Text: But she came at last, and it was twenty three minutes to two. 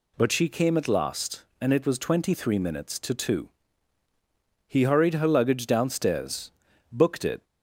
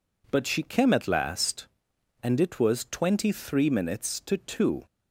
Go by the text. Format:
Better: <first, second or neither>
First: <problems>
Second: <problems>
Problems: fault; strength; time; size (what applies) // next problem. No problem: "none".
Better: second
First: goes on to say "He hurried her luggage downstairs booked it"; strong; from 4.6 s on; 2.7 s long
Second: none